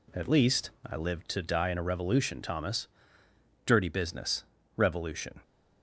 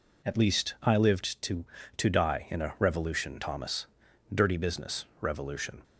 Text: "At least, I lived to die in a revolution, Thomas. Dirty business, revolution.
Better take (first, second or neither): first